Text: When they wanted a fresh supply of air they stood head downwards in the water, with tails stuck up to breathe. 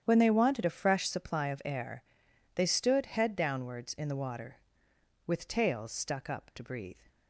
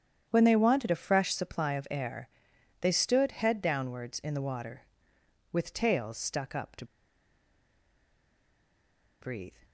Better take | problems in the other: first | starts louder than the rest; strong; until 1.3 s; 9 dB; strong in the first // pauses between "air" and "they"; noticeable; at 2.2 s; 0.54 s long; noticeable in the first // pauses between "to" and "breathe"; strong; at 6.8 s; 2.3 s long

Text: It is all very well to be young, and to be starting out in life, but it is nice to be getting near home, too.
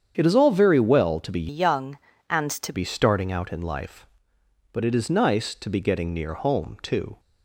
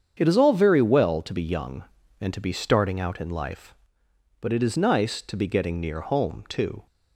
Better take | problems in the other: second | starts louder than the rest; strong; until 1.1 s; 8 dB; strong in the second // changes voice from "young" to "to"; from 1.4 to 2.7 s; 1.3 s long

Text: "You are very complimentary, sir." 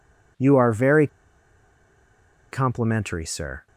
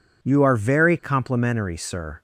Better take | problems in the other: second | pauses between "very" and "complimentary"; strong; at 1.0 s; 1.4 s long

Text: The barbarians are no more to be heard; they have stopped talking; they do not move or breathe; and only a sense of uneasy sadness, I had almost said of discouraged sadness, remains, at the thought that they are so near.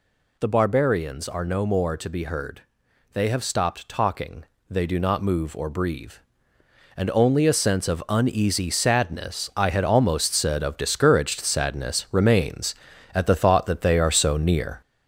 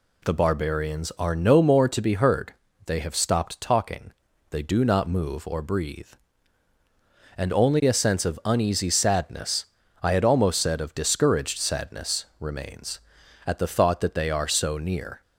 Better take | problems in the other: second | gets louder; noticeable; throughout; 4.5 dB

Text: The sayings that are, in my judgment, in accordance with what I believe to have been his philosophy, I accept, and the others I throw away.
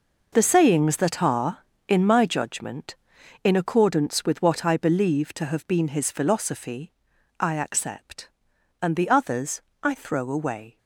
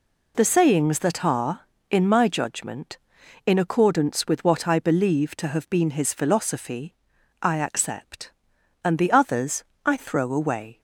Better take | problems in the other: second | gets quieter; strong; throughout; 11.5 dB // pauses between "others" and "I"; slight; at 9.6 s; 0.22 s long; slight in the second

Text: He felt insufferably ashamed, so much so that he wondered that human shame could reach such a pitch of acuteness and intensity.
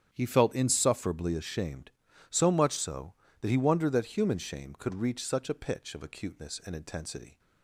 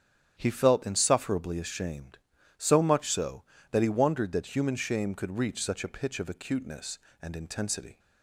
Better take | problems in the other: neither | starts louder than the rest; strong; the same in both

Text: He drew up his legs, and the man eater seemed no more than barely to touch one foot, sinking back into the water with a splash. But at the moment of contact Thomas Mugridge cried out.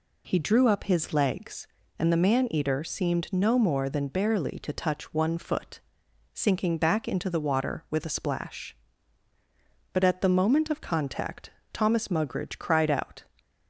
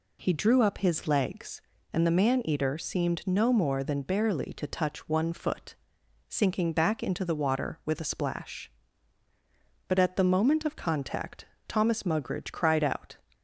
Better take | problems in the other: neither | pauses between "contact" and "Thomas"; slight; the same in both

